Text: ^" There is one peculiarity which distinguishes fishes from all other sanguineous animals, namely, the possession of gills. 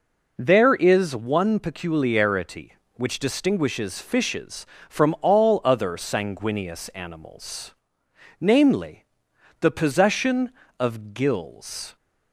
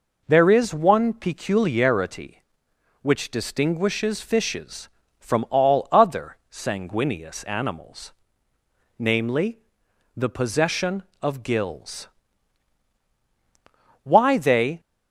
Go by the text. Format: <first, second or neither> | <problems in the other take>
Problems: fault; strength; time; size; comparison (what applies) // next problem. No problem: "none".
first | goes on to say "Why they"; noticeable; from 14.0 s on; 0.76 s long